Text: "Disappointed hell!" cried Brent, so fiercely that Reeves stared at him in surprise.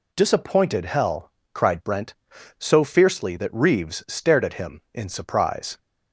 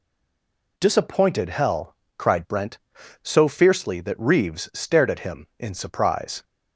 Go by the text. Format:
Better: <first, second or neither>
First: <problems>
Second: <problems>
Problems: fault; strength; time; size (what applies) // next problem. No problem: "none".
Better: first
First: none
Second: stays silent before the first word; slight; until 0.7 s; 0.7 s long